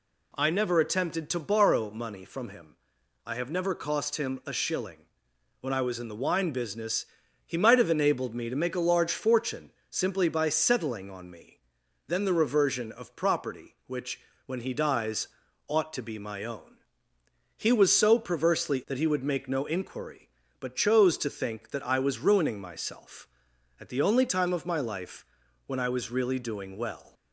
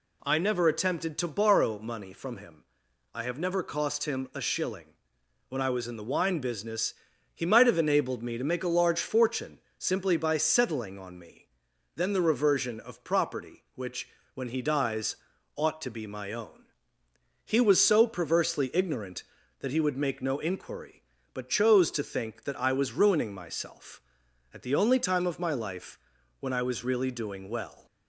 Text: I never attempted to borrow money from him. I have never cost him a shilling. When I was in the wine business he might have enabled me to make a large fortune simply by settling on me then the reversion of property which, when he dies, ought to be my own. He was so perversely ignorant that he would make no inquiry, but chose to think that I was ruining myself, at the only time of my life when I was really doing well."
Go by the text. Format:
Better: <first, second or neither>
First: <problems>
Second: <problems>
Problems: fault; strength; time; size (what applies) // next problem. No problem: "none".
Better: second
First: pauses between "business" and "he"; at 7.0 s; 0.40 s long // pauses between "fortune" and "simply"; slight; at 9.6 s; 0.22 s long // pauses between "me" and "then"; noticeable; at 11.5 s; 0.50 s long // skips "ignorant"; at 18.8 s // pauses between "life" and "when"; at 25.2 s; 0.40 s long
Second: pauses between "business" and "he"; at 6.9 s; 0.40 s long // pauses between "fortune" and "simply"; slight; at 9.5 s; 0.22 s long // pauses between "me" and "then"; noticeable; at 11.4 s; 0.50 s long // pauses between "life" and "when"; at 25.9 s; 0.40 s long